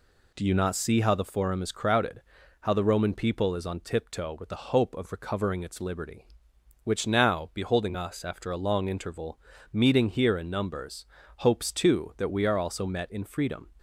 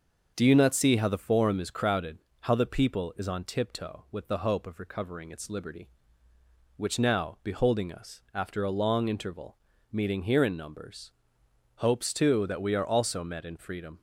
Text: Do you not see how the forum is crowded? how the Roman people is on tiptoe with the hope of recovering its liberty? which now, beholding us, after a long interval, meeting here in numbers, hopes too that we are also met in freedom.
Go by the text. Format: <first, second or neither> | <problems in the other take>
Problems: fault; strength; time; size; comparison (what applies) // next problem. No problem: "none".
first | starts louder than the rest; until 1.3 s; 6.5 dB // skips "Roman"; at 2.6 s